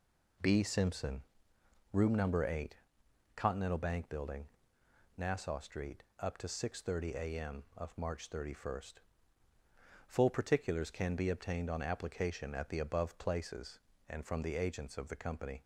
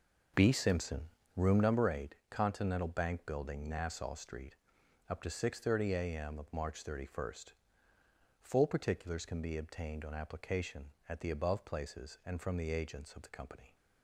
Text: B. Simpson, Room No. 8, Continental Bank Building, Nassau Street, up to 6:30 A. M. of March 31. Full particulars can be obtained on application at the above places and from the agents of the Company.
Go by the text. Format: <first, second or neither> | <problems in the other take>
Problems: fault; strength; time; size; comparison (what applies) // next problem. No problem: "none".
first | starts louder than the rest; until 2.0 s; 6.5 dB